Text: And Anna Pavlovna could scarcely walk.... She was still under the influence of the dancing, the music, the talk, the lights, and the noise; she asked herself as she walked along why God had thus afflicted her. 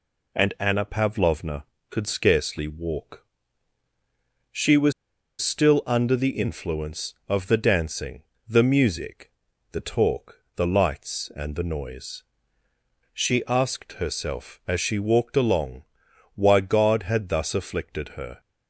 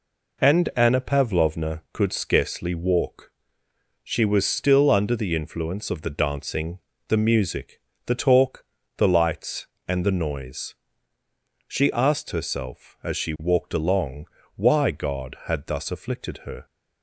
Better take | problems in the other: second | pauses between "was" and "still"; noticeable; at 4.9 s; 0.49 s long // pauses between "along" and "why"; noticeable; at 15.8 s; 0.50 s long; slight in the second

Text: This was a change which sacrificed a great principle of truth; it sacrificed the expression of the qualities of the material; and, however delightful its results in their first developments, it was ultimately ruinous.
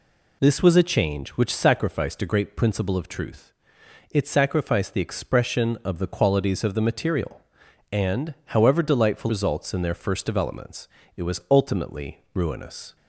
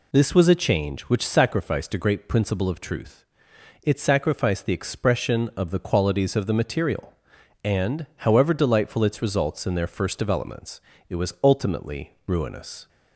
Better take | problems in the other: second | skips "its"; at 9.2 s

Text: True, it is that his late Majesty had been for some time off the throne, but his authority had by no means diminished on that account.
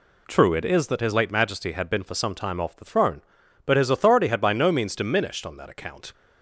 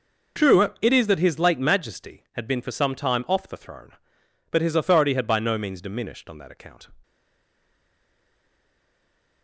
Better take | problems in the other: first | stays silent after the last word; from 7.0 s on; 2.4 s long

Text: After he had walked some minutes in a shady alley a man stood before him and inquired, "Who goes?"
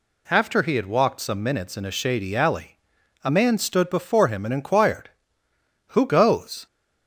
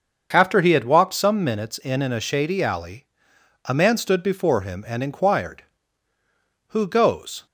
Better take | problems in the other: first | starts louder than the rest; until 1.3 s; 6.5 dB // says "in" twice; at 2.0 s // pauses between "alley" and "a"; noticeable; at 3.0 s; 0.58 s long; also in the first

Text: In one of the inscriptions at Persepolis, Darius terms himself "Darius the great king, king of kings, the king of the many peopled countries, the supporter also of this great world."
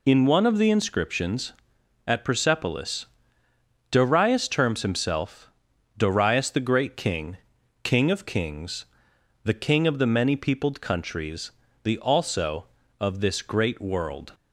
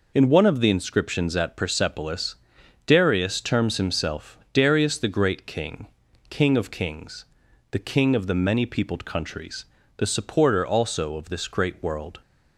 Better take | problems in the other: second | pauses between "himself" and "Darius"; noticeable; at 5.5 s; 0.46 s long // skips "supporter"; at 11.9 s

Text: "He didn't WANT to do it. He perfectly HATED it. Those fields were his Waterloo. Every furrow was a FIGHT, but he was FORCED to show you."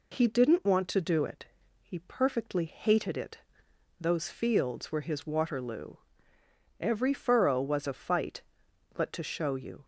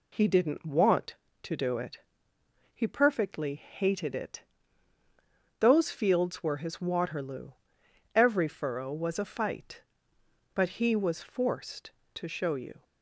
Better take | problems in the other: second | skips "he was FORCED"; at 9.1 s

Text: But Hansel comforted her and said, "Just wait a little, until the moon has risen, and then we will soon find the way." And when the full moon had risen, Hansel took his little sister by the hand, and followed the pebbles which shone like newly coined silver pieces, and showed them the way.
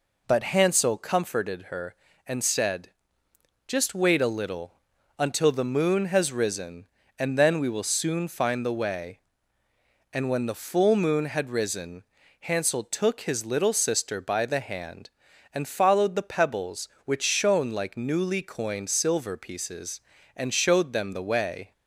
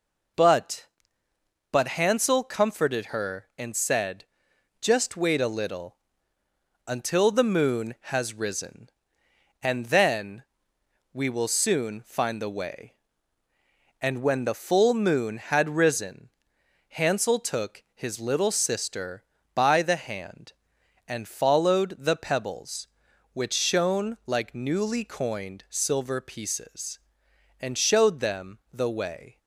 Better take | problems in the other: first | says "But" twice; at 1.7 s // pauses between "then" and "we"; noticeable; at 10.4 s; 0.68 s long

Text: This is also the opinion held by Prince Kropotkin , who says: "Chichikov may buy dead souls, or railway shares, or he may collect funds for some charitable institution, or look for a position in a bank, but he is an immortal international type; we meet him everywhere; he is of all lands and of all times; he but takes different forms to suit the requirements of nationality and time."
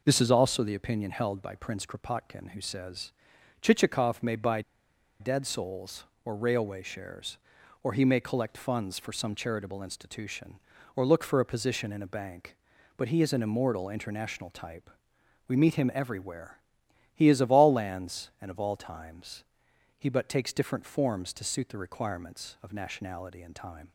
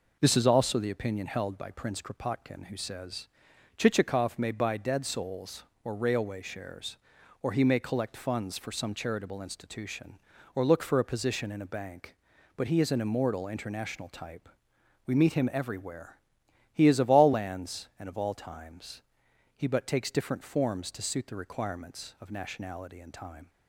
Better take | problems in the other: second | pauses between "buy" and "dead"; noticeable; at 4.6 s; 0.59 s long

